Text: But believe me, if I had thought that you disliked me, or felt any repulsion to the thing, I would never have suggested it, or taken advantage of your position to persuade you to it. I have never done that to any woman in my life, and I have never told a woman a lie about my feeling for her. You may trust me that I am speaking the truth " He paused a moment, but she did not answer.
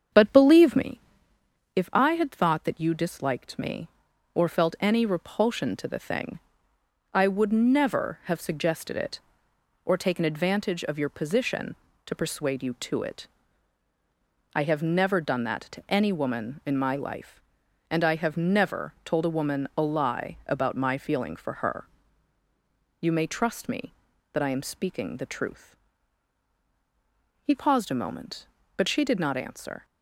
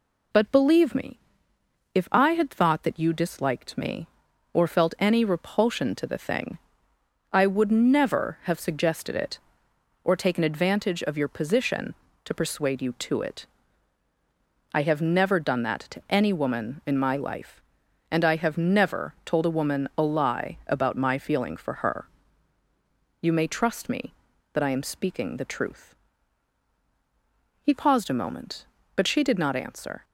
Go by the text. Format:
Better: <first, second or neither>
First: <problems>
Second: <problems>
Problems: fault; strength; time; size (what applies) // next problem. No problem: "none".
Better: second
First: starts louder than the rest; strong; until 1.7 s; 7.5 dB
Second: none